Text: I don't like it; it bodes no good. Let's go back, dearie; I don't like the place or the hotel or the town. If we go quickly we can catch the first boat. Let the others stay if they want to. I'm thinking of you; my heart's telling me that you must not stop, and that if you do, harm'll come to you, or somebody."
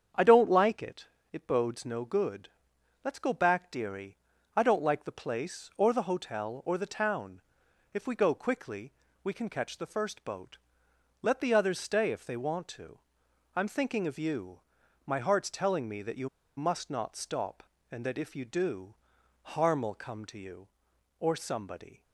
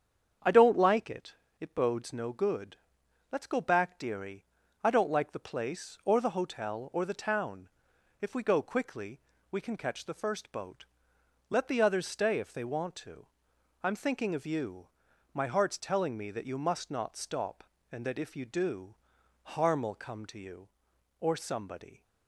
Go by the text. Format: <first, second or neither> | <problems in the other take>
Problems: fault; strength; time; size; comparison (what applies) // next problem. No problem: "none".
second | starts louder than the rest; strong; until 1.4 s; 7.5 dB; strong in the second // pauses between "quickly" and "we"; slight; at 8.9 s; 0.30 s long; slight in the second // pauses between "you" and "must"; slight; at 16.2 s; 0.28 s long